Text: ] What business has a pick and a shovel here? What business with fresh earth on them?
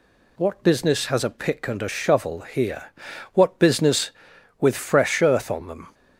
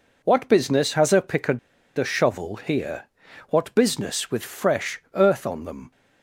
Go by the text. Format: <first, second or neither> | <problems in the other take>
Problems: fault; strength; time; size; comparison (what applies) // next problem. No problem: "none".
first | pauses between "and" and "a"; at 1.5 s; 0.39 s long